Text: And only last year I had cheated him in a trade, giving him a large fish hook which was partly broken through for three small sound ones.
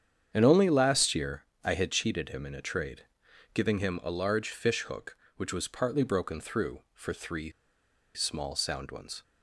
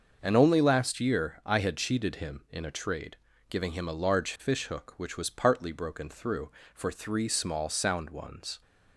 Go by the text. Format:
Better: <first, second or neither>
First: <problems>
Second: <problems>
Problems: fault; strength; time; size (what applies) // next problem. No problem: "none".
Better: second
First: starts louder than the rest; strong; until 1.3 s; 8 dB // pauses between "year" and "I"; slight; at 1.4 s; 0.18 s long // pauses between "three" and "small"; noticeable; at 7.4 s; 0.65 s long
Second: starts louder than the rest; until 1.2 s; 6.5 dB